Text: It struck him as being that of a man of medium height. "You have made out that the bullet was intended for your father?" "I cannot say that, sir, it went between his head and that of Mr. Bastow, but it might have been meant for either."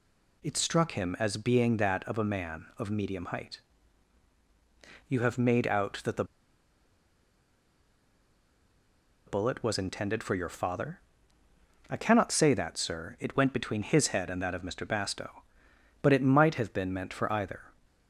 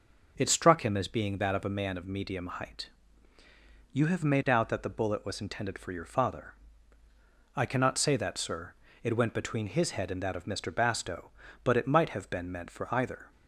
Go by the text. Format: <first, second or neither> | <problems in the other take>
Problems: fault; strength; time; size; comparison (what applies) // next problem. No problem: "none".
second | pauses between "the" and "bullet"; strong; at 6.2 s; 3.0 s long